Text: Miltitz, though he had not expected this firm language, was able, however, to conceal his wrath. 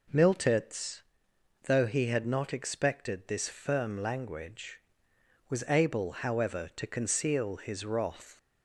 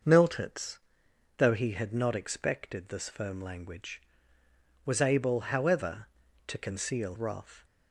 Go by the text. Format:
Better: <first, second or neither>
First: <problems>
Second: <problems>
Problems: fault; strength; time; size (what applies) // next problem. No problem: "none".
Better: first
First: none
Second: starts louder than the rest; noticeable; until 1.6 s; 6 dB // skips "his"; at 7.1 s